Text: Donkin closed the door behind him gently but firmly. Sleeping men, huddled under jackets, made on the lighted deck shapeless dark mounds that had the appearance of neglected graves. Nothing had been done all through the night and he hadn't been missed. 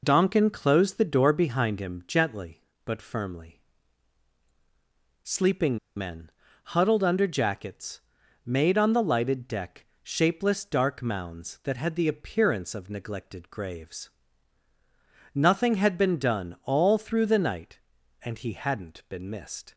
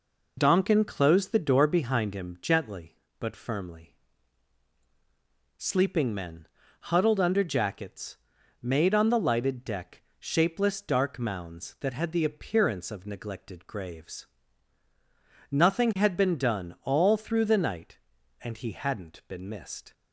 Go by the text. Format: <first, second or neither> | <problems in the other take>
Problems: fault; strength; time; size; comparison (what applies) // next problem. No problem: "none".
second | pauses between "Sleeping" and "men"; slight; at 5.7 s; 0.19 s long // pauses between "deck" and "shapeless"; slight; at 9.8 s; 0.18 s long; slight in the second